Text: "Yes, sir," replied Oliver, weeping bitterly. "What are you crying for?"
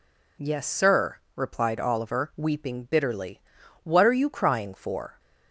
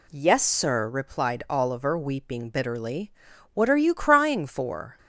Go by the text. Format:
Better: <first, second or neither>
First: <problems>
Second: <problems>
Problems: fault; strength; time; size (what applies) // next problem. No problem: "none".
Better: neither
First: none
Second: none